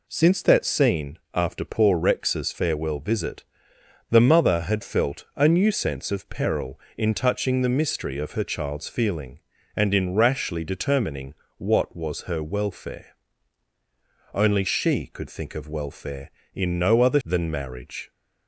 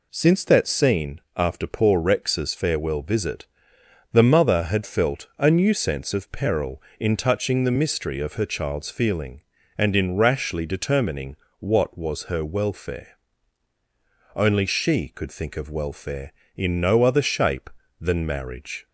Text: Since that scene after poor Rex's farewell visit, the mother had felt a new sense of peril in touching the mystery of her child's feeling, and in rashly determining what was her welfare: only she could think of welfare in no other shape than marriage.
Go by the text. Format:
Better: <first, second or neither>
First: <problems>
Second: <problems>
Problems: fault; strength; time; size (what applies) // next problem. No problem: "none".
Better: second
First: pauses between "scene" and "after"; slight; at 1.1 s; 0.16 s long // pauses between "determining" and "what"; slight; at 11.3 s; 0.22 s long // skips "shape"; at 17.2 s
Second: pauses between "scene" and "after"; slight; at 1.2 s; 0.16 s long // pauses between "determining" and "what"; slight; at 11.3 s; 0.22 s long